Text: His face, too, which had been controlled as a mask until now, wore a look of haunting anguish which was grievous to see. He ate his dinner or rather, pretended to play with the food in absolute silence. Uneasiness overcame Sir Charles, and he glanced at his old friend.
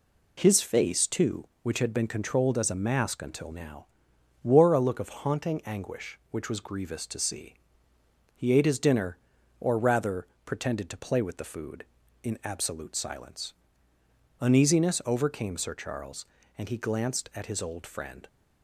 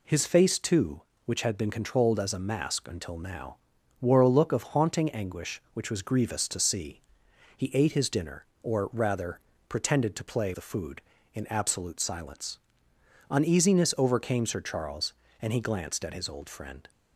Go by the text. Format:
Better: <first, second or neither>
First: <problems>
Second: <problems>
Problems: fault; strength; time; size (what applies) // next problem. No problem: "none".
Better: first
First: none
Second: skips "with"; at 10.5 s